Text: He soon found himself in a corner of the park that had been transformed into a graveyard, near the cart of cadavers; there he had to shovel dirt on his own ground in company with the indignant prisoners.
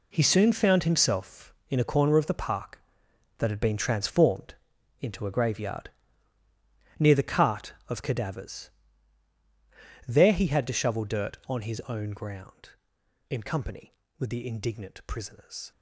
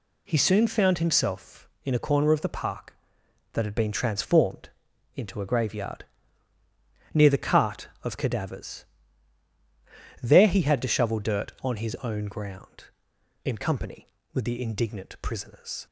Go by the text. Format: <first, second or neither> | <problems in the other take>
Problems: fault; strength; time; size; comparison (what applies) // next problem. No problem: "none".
second | gets quieter; strong; throughout; 10.5 dB // pauses between "transformed" and "into"; at 4.5 s; 0.44 s long; also in the second